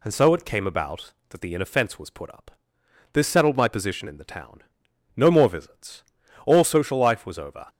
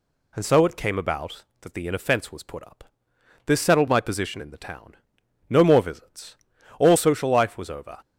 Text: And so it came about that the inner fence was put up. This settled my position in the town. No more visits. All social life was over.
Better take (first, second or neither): neither